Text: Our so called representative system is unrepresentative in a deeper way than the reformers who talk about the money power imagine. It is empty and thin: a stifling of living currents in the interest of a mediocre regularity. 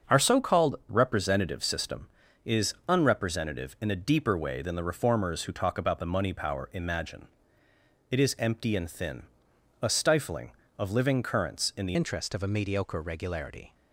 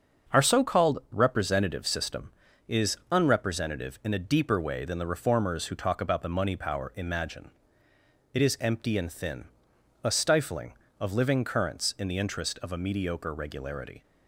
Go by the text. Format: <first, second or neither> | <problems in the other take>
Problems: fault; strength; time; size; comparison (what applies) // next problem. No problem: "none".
second | starts louder than the rest; until 1.2 s; 6.5 dB; also in the second // changes voice at "interest"; from 11.9 s on; 1.8 s long